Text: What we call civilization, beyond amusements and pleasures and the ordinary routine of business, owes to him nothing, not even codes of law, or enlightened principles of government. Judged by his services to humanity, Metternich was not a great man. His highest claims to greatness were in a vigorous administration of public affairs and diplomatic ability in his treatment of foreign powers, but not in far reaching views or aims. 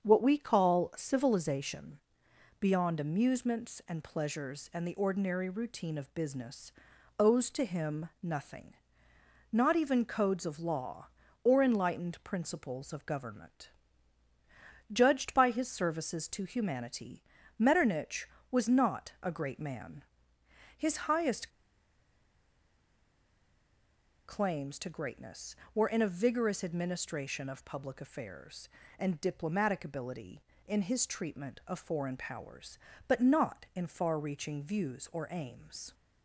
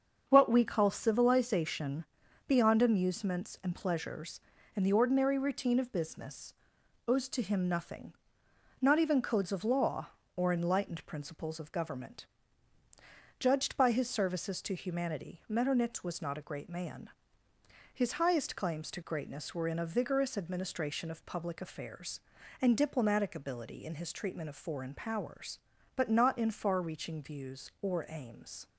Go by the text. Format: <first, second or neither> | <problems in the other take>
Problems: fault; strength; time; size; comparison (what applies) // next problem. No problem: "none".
second | starts louder than the rest; strong; until 1.0 s; 7 dB; also in the second // pauses between "highest" and "claims"; strong; at 21.5 s; 2.7 s long